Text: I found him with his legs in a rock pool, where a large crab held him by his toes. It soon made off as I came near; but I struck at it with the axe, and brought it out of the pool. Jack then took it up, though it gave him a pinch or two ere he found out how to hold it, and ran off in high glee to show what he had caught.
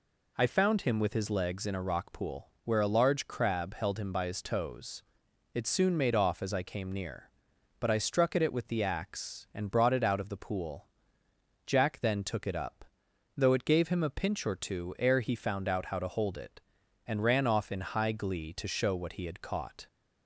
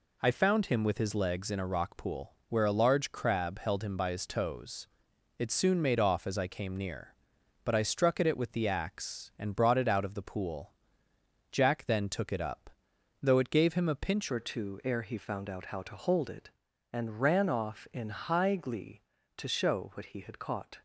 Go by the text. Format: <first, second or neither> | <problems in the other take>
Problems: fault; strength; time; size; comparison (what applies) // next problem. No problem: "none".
first | changes voice at "or"; from 14.2 s on; 6.6 s long